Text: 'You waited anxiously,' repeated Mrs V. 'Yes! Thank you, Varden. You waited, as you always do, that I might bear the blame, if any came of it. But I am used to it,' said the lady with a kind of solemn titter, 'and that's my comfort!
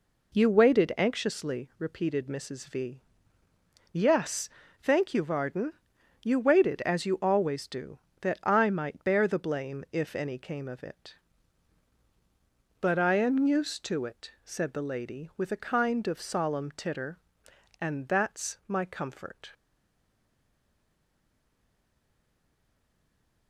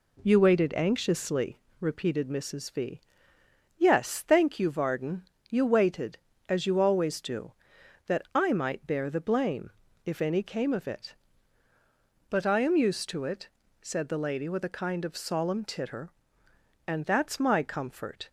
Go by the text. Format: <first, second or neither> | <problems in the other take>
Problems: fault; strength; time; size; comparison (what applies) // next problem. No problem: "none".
second | stays silent after the last word; strong; from 19.5 s on; 3.9 s long